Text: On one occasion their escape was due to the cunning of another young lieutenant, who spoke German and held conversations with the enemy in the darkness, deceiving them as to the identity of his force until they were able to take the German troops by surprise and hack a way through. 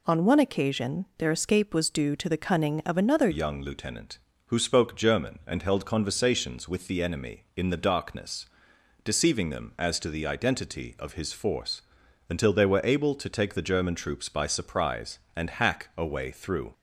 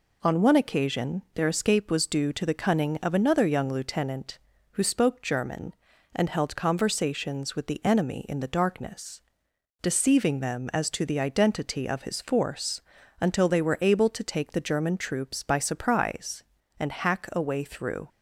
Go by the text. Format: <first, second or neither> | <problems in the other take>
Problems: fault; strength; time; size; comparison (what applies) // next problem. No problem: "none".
second | changes voice at "young"; from 3.3 s on; 13.4 s long // pauses between "force" and "until"; noticeable; at 11.8 s; 0.48 s long; also in the second